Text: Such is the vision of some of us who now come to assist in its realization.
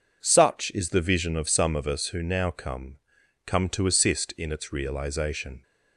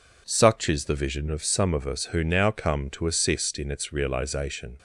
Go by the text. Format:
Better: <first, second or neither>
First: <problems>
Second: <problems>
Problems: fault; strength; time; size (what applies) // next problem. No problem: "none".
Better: second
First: says "come" twice; at 3.4 s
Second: none